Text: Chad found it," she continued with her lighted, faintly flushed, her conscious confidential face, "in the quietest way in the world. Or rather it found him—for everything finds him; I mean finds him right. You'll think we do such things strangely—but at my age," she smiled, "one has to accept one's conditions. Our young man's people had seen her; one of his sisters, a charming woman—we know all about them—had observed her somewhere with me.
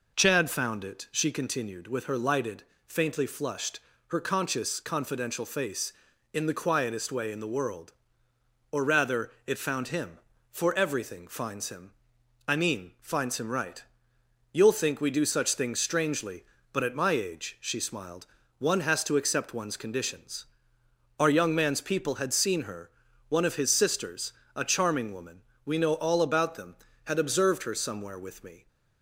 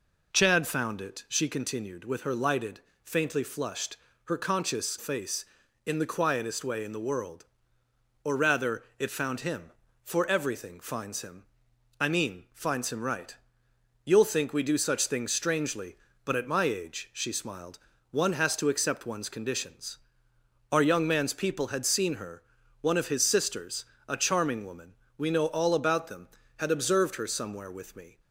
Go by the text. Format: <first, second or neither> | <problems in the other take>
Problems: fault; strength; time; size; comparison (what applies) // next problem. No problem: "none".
first | skips "confidential"; at 4.9 s // pauses between "rather" and "it"; slight; at 8.8 s; 0.16 s long; slight in the first